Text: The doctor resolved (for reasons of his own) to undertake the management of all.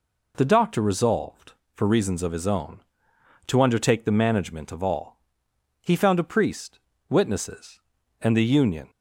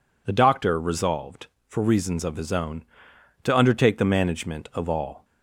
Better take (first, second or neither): second